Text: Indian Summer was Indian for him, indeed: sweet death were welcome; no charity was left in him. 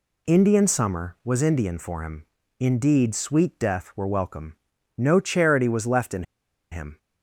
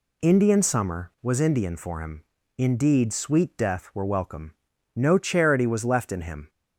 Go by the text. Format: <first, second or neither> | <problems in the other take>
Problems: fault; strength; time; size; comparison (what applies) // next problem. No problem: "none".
second | pauses between "in" and "him"; noticeable; at 6.2 s; 0.48 s long